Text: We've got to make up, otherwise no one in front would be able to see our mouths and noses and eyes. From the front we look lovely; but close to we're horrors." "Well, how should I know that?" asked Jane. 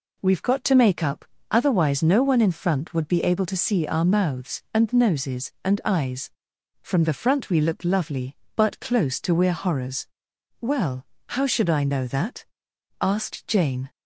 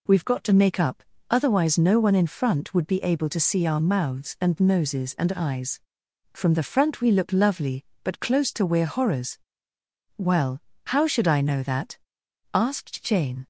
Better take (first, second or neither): neither